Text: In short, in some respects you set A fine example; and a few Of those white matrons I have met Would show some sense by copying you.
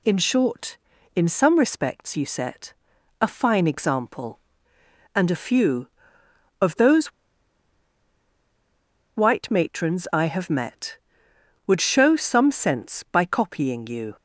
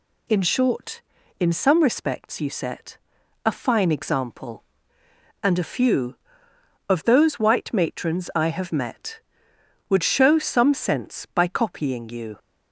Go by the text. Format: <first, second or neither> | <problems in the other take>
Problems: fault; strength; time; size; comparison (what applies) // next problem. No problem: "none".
second | pauses between "set" and "A"; noticeable; at 2.7 s; 0.48 s long; noticeable in the second // pauses between "those" and "white"; strong; at 7.1 s; 2.0 s long